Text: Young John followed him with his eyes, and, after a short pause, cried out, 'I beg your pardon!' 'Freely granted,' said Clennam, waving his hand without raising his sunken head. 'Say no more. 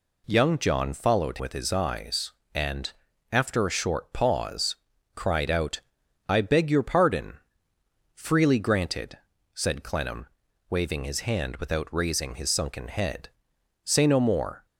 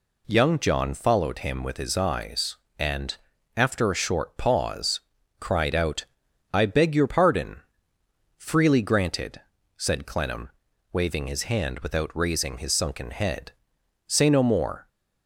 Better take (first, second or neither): second